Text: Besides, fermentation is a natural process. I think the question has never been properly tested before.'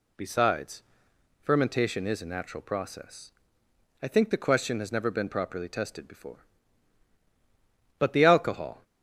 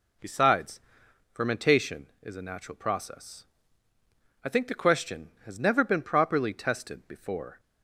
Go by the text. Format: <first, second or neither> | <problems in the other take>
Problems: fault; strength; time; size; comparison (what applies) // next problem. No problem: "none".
second | goes on to say "But the alcohol"; noticeable; from 7.9 s on; 0.86 s long